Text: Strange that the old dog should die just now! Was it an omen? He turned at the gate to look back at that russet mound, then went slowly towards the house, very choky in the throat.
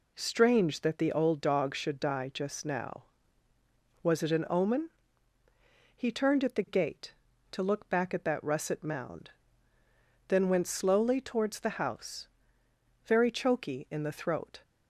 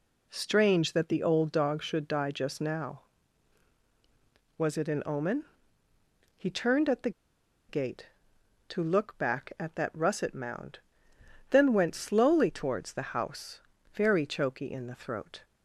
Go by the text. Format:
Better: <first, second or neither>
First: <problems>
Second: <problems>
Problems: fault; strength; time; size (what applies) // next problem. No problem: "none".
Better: first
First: none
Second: pauses between "the" and "gate"; noticeable; at 7.1 s; 0.58 s long